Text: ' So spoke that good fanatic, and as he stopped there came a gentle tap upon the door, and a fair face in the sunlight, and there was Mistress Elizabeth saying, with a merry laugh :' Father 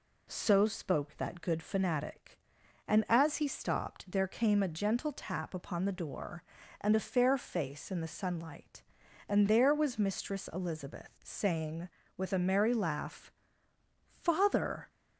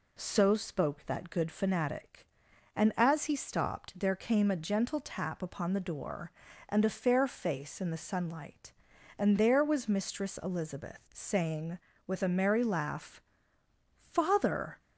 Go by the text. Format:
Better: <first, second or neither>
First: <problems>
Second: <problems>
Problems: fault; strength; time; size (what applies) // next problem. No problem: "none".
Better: neither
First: none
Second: none